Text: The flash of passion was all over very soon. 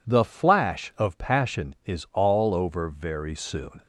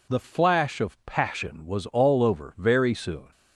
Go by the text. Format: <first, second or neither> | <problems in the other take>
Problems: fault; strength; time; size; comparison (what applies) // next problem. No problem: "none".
second | says "is" for "was"; at 1.8 s